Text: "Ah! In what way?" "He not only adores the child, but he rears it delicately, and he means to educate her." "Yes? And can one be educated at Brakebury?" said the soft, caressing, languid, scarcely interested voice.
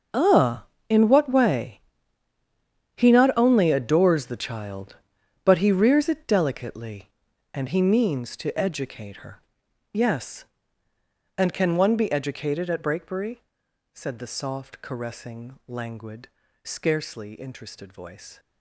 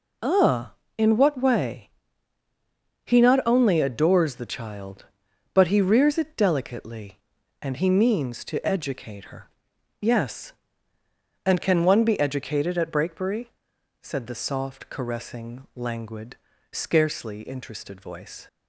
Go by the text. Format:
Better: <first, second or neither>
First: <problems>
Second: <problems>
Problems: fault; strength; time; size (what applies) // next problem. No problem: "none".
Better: second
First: gets quieter; strong; throughout; 14.5 dB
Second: none